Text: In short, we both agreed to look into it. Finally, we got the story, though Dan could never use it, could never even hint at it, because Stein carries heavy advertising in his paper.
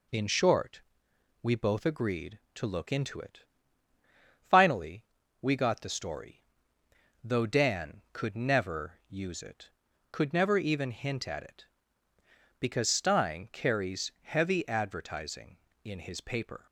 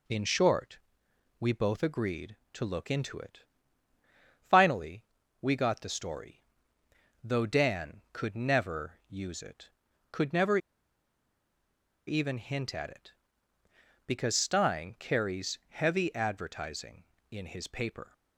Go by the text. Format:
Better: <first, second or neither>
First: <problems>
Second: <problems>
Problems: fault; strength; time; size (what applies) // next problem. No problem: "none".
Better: first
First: none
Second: pauses between "never" and "even"; strong; at 10.5 s; 1.4 s long